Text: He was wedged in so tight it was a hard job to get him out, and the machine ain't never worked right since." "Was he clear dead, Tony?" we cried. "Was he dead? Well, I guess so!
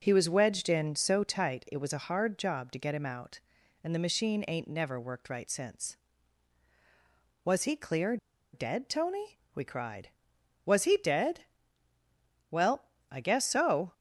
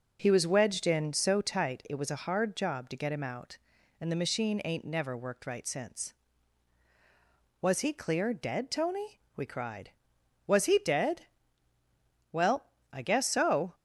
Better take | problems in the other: second | pauses between "clear" and "dead"; at 8.1 s; 0.36 s long

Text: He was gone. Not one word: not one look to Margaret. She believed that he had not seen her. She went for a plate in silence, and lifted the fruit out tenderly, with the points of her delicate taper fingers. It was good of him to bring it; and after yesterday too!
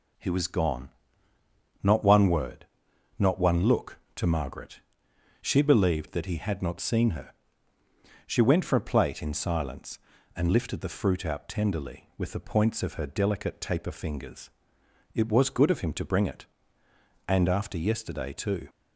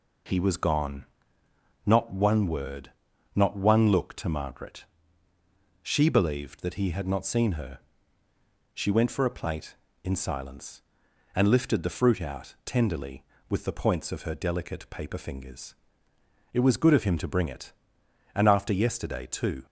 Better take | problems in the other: first | says "paper" for "taper"; at 14.8 s

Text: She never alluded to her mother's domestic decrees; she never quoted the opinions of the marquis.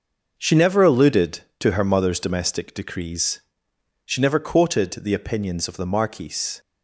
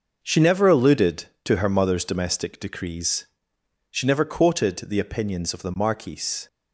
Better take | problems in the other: neither | none

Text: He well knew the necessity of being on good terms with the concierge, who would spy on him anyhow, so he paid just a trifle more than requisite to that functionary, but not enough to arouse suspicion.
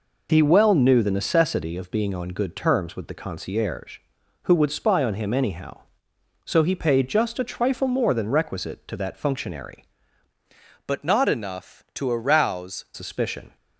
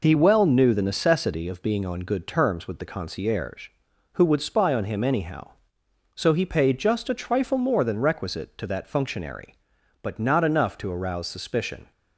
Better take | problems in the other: second | changes voice from "but" to "arouse"; from 10.8 to 12.8 s; 2.0 s long

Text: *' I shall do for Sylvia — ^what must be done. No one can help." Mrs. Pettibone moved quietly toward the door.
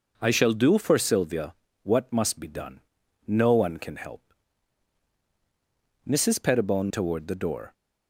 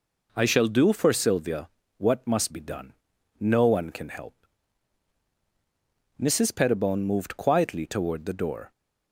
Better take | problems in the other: second | skips "moved quietly"; at 6.8 s

